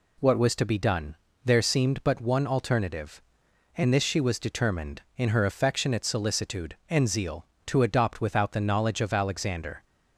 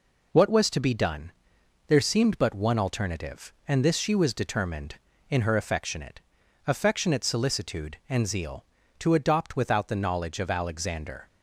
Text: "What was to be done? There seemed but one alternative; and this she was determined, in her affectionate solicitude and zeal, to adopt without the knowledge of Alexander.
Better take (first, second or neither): first